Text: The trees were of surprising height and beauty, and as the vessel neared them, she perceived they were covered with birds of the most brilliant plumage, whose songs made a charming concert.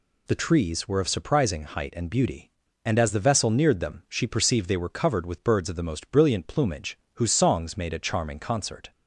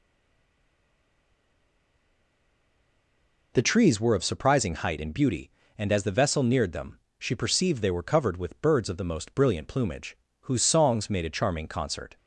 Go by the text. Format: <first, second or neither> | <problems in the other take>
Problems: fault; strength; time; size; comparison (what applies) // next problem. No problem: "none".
first | stays silent before the first word; strong; until 3.5 s; 3.5 s long